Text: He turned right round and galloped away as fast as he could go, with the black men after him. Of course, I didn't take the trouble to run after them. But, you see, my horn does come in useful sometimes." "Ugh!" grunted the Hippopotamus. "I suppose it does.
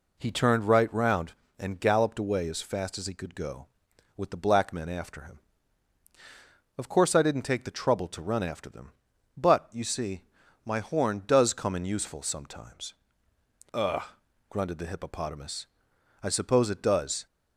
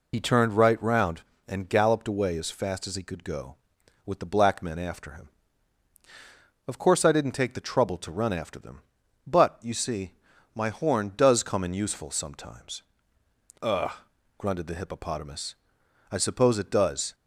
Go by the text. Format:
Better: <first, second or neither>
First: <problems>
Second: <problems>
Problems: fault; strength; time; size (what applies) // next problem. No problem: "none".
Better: first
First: none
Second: loses the start of "He"; at 0.1 s; 60 ms